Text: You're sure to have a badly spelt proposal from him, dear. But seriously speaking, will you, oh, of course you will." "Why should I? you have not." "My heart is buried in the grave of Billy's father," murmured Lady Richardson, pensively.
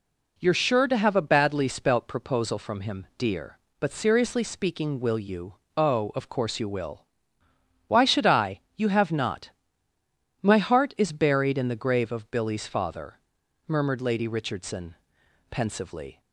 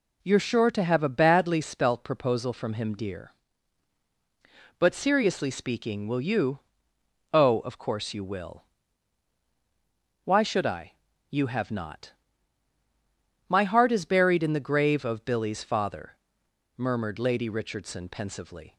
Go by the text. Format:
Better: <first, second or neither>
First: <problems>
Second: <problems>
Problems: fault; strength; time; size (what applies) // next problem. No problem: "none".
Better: neither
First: none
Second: none